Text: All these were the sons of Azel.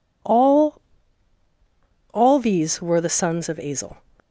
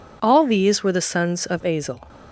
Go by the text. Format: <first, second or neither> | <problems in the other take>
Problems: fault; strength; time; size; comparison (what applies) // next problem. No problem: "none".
second | says "All" twice; at 2.1 s